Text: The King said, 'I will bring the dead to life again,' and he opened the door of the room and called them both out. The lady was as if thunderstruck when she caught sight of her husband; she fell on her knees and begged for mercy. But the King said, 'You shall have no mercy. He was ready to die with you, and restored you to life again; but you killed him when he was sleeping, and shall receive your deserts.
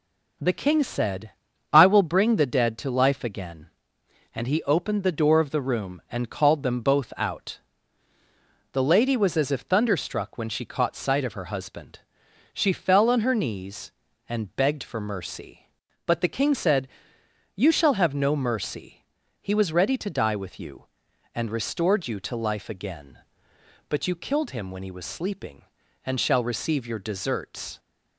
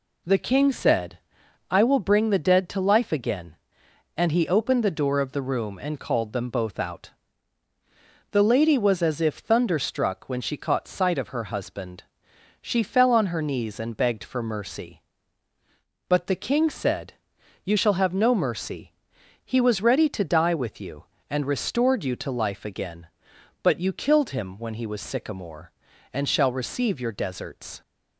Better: first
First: none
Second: says "sycamore" for "sleeping"; at 25.0 s

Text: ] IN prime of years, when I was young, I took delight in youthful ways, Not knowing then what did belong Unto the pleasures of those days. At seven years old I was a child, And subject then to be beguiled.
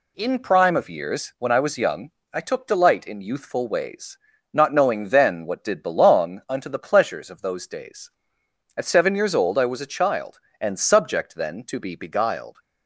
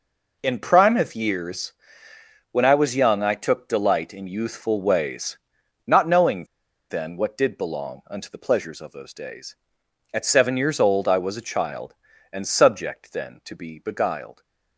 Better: first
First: none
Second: pauses between "knowing" and "then"; at 6.4 s; 0.45 s long

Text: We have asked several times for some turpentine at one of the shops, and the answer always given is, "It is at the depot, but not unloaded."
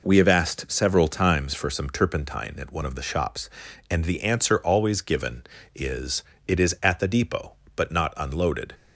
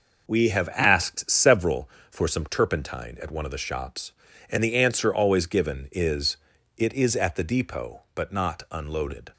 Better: first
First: none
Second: skips "times"; at 1.9 s

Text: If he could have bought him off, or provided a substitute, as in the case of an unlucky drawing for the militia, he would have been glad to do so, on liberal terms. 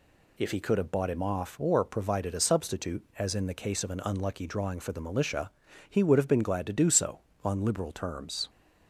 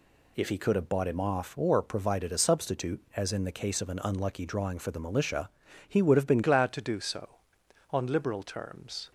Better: first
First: none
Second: changes voice at "glad"; from 6.4 s on; 2.7 s long

